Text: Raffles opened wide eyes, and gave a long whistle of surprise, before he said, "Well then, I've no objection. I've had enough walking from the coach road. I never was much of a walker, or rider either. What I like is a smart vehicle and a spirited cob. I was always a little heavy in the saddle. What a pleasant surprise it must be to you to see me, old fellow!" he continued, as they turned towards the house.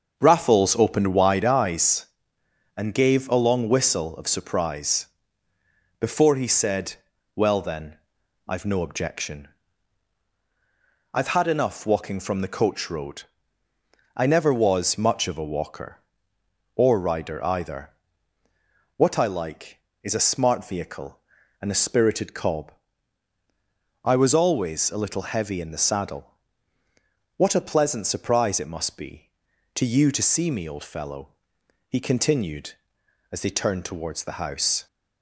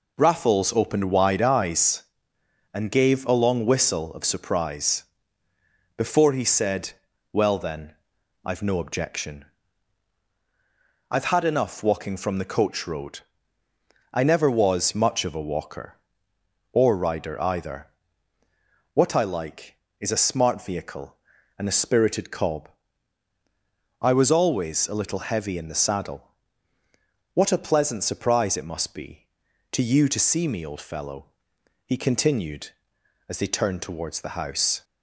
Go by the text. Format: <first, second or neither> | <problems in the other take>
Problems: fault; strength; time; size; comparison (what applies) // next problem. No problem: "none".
second | starts louder than the rest; until 1.4 s; 6.5 dB